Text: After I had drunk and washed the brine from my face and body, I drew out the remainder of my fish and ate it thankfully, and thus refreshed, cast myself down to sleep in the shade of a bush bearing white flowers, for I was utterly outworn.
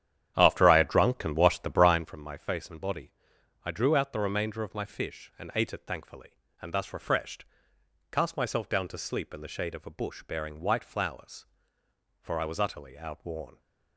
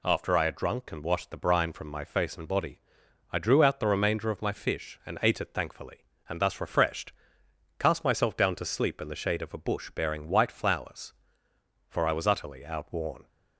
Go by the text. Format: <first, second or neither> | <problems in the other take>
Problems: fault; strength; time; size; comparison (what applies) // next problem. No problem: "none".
second | starts louder than the rest; strong; until 2.1 s; 10 dB